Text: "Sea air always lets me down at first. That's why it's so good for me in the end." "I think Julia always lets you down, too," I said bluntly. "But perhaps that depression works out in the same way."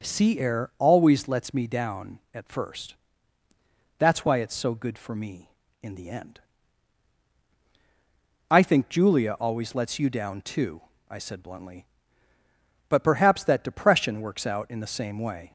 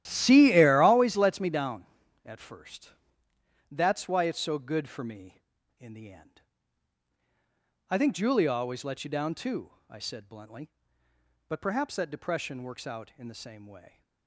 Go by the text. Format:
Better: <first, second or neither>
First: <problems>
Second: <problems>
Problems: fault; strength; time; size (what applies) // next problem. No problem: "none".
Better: first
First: none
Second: starts louder than the rest; strong; until 1.1 s; 13 dB